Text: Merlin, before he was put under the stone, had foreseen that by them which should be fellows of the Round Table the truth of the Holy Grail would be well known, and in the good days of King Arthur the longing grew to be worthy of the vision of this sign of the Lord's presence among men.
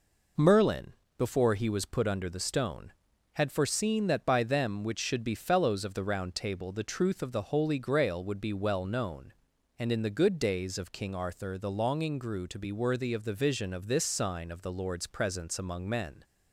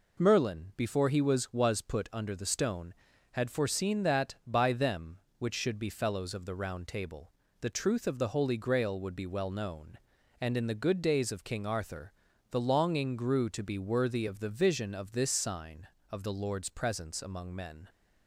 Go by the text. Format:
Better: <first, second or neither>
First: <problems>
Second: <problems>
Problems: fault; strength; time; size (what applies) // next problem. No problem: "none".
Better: first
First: none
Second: says "was" twice; at 1.5 s // pauses between "Table" and "the"; slight; at 7.3 s; 0.30 s long // pauses between "Arthur" and "the"; slight; at 12.1 s; 0.36 s long